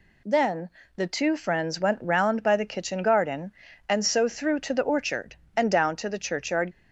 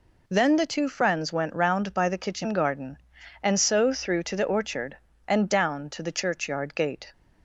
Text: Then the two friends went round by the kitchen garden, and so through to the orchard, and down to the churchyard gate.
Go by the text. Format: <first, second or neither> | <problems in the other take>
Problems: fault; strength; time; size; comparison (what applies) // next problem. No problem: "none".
second | pauses between "Then" and "the"; slight; at 0.6 s; 0.30 s long // stops before "gate"; at 6.7 s